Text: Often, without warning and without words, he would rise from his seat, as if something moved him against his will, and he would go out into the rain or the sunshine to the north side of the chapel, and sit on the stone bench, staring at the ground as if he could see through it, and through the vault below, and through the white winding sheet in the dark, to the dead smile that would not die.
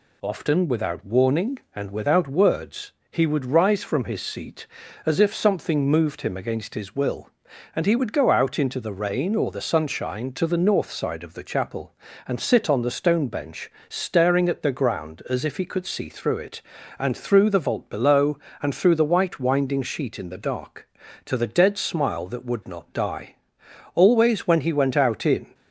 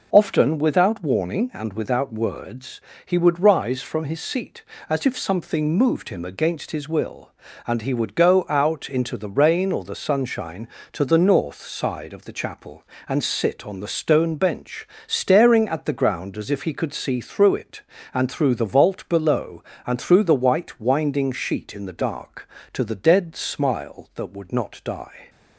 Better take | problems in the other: second | goes on to say "Always when he went out in"; from 23.9 s on; 1.6 s long

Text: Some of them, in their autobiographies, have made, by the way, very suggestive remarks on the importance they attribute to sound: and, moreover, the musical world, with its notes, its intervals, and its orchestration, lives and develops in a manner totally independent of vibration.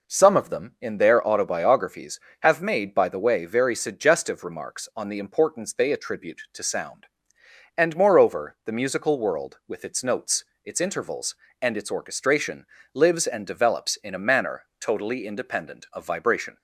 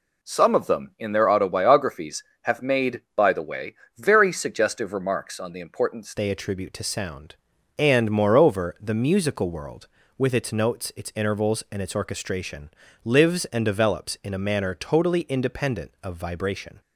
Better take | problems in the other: first | changes voice at "they"; from 6.1 s on; 10.7 s long

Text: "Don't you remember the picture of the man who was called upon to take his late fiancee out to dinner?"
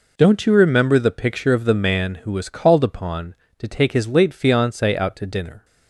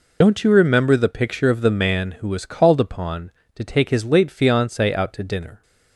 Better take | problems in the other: first | loses the start of "Don't"; at 0.2 s; 50 ms

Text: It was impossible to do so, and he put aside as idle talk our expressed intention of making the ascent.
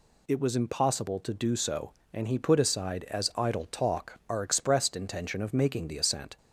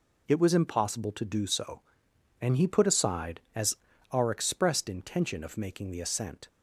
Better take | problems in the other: first | skips "idle talk"; at 3.9 s

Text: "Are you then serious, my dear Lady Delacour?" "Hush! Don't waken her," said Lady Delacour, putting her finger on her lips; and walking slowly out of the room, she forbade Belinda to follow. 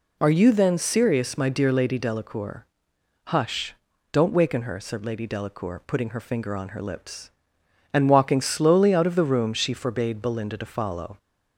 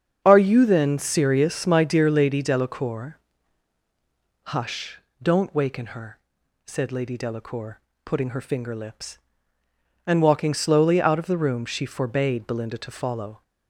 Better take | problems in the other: first | starts louder than the rest; strong; until 1.2 s; 7 dB // skips "on her"; at 8.7 s

